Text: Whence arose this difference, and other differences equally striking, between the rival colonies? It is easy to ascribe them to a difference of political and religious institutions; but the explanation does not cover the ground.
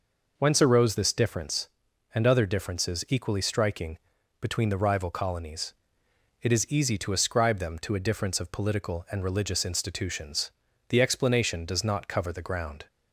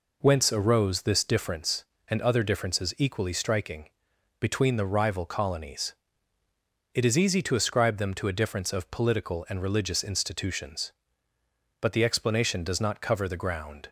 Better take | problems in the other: second | skips "but"; at 10.6 s

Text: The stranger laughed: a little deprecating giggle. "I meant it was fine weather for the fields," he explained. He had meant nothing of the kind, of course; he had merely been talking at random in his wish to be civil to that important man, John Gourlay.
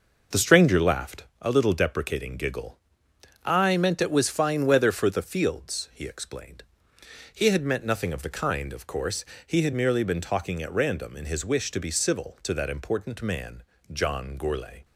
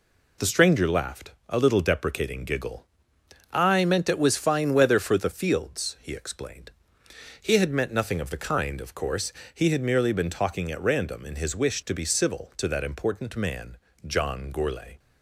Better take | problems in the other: second | starts louder than the rest; noticeable; until 1.3 s; 5.5 dB

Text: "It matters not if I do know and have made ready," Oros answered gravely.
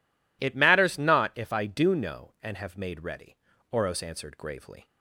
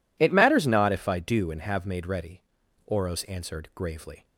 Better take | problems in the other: first | skips "know"; at 1.5 s

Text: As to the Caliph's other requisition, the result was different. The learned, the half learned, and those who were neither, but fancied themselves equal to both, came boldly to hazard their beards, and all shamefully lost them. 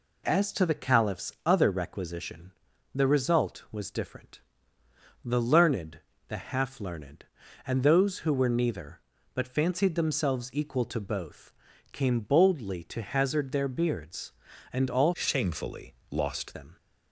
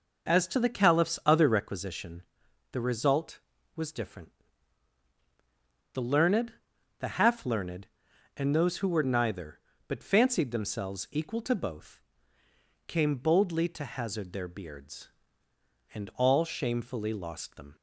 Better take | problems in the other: second | changes voice from "shamefully" to "lost"; from 15.1 to 16.5 s; 1.4 s long // pauses between "shamefully" and "lost"; slight; at 15.9 s; 0.18 s long

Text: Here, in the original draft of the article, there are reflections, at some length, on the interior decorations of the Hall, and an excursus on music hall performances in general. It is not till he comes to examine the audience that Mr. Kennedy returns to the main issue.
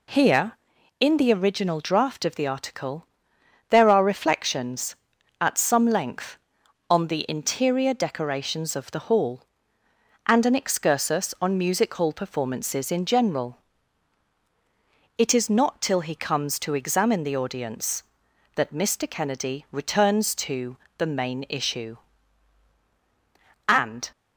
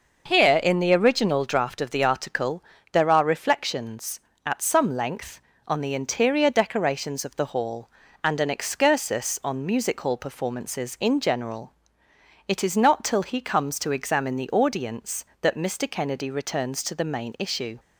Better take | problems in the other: second | pauses between "to" and "the"; slight; at 20.7 s; 0.20 s long // goes on to say "And"; slight; from 23.6 s on; 0.42 s long

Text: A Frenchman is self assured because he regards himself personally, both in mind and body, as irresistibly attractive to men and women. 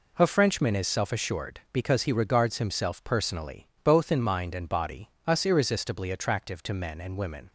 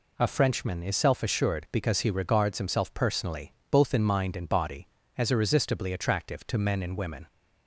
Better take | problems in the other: second | says "us" for "as"; at 5.2 s

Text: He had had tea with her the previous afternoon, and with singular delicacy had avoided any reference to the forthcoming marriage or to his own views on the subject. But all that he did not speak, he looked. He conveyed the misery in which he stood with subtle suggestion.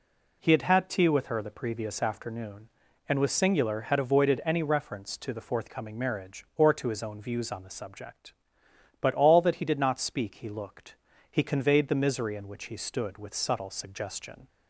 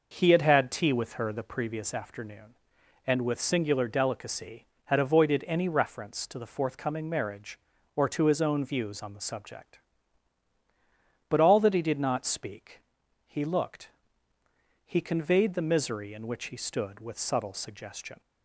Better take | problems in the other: second | skips "delicacy"; at 3.8 s

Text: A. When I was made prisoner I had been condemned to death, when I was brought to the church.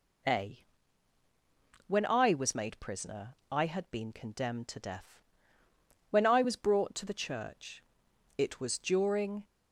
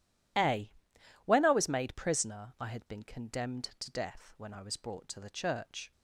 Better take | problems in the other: second | pauses between "prisoner" and "I"; slight; at 3.3 s; 0.16 s long // goes on to say "It was during"; noticeable; from 8.3 s on; 1.0 s long

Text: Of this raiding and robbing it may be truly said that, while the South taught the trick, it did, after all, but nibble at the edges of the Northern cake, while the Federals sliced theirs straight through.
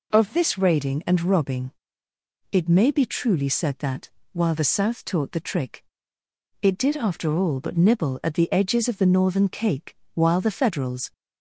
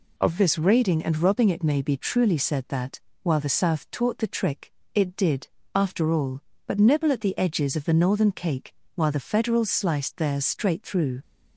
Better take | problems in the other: second | pauses between "robbing" and "it"; noticeable; at 1.7 s; 0.80 s long // stops before "sliced theirs straight through"; at 11.1 s

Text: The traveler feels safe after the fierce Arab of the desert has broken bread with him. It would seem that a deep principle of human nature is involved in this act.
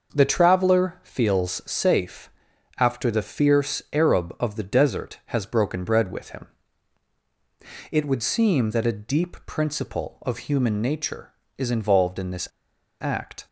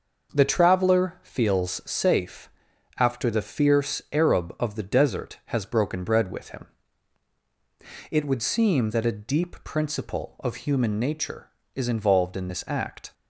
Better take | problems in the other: second | pauses between "safe" and "after"; noticeable; at 2.2 s; 0.48 s long; noticeable in the second // pauses between "this" and "act"; noticeable; at 12.4 s; 0.51 s long

